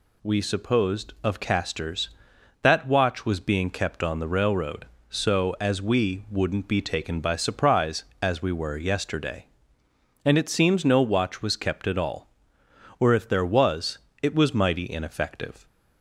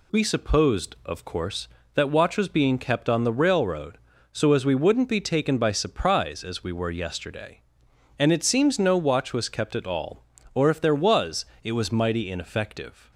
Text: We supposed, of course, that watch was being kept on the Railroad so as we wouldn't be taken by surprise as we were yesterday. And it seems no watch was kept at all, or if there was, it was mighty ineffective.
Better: second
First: says "casters" for "course"; at 1.3 s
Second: none

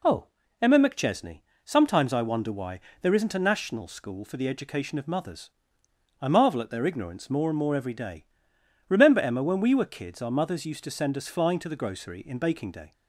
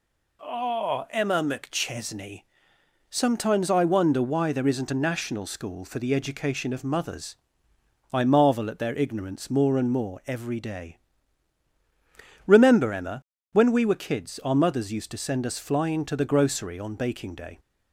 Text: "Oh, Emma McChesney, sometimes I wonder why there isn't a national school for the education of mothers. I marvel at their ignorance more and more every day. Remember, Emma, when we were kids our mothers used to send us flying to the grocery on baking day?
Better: second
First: pauses between "why" and "there"; slight; at 2.7 s; 0.22 s long // says "in" for "on"; at 12.1 s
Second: none

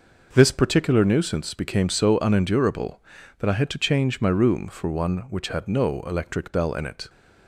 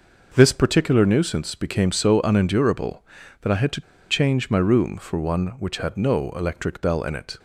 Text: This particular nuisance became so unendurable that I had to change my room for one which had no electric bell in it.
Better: first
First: none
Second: pauses between "to" and "change"; slight; at 3.8 s; 0.28 s long

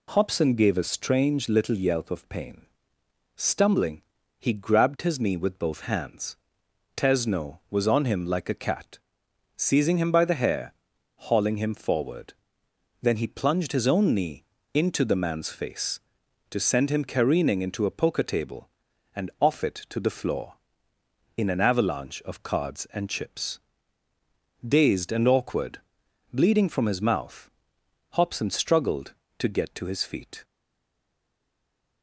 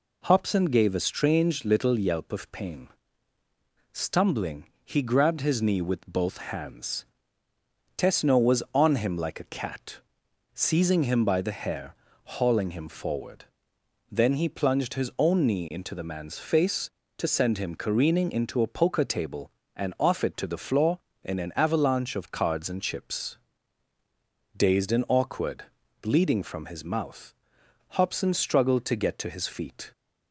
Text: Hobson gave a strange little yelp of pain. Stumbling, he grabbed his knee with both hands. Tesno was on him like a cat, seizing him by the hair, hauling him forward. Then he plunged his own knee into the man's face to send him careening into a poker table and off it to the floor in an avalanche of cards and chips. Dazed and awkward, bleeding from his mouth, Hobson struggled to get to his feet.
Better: second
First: pauses between "knee" and "into"; slight; at 14.4 s; 0.30 s long // stays silent after the last word; noticeable; from 30.4 s on; 1.6 s long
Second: none

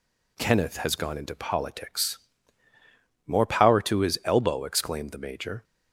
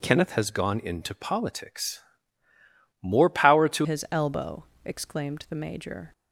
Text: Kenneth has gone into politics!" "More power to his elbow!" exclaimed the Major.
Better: first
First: none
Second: changes voice at "his"; from 3.8 s on; 2.3 s long

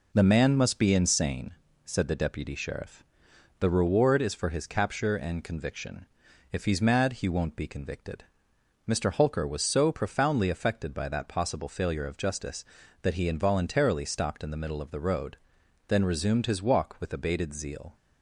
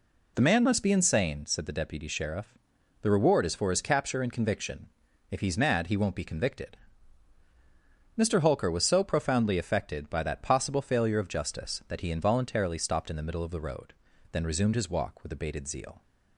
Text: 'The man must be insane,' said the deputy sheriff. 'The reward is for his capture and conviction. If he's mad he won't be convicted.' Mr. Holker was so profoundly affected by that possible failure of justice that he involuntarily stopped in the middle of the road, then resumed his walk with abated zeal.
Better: neither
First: none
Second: none

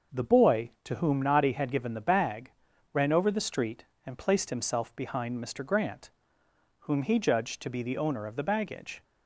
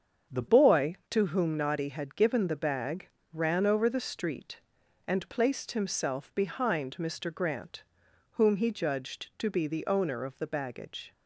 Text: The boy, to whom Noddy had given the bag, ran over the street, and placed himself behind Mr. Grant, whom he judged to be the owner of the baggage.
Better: first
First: starts louder than the rest; noticeable; until 1.2 s; 6 dB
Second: starts louder than the rest; strong; until 1.4 s; 7.5 dB // changes voice at "boy"; from 0.4 s on; 10.7 s long

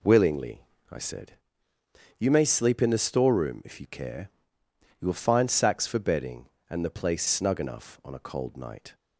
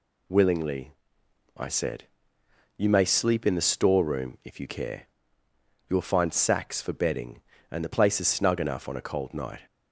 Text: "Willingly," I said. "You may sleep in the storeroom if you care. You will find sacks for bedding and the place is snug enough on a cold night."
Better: second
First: skips "is"; at 7.2 s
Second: none

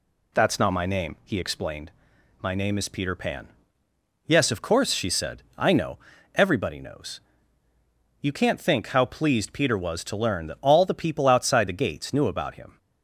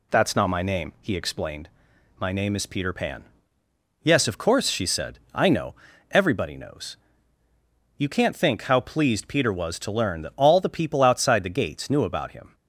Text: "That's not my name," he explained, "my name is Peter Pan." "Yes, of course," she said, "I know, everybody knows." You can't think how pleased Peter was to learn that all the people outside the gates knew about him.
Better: neither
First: none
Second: none

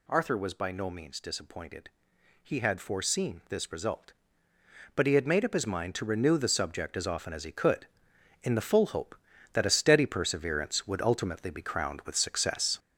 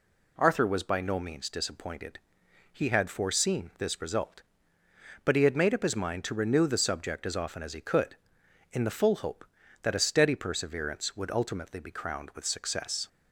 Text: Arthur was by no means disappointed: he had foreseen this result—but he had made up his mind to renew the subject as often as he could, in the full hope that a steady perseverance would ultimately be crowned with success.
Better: second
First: gets louder; noticeable; throughout; 6 dB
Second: none

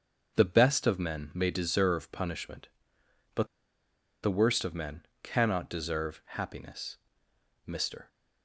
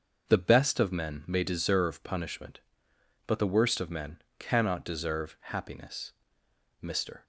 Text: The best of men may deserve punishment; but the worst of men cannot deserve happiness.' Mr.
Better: second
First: starts louder than the rest; until 1.4 s; 6.5 dB // pauses between "but" and "the"; noticeable; at 3.4 s; 0.77 s long // pauses between "men" and "cannot"; slight; at 5.0 s; 0.16 s long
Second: starts louder than the rest; until 1.3 s; 6.5 dB // pauses between "men" and "cannot"; slight; at 4.2 s; 0.16 s long

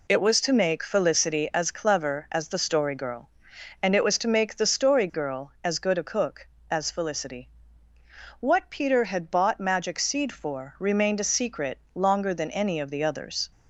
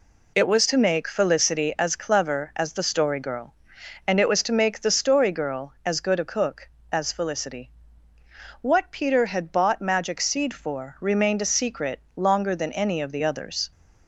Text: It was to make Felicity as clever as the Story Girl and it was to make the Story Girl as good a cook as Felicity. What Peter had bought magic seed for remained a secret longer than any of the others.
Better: neither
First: none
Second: none

